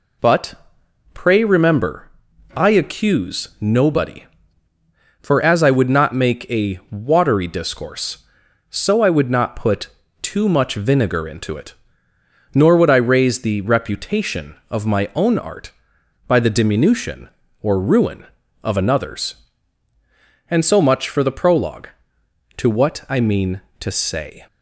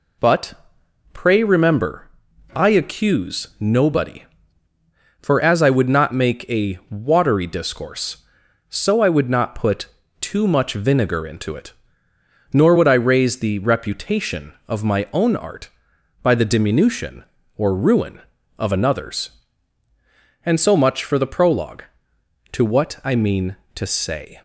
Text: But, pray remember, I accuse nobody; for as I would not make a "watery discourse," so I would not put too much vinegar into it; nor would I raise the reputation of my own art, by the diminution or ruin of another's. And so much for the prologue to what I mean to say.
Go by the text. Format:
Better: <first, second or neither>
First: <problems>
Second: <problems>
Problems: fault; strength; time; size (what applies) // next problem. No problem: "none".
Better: neither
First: pauses between "put" and "too"; slight; at 9.8 s; 0.34 s long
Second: pauses between "put" and "too"; slight; at 9.8 s; 0.34 s long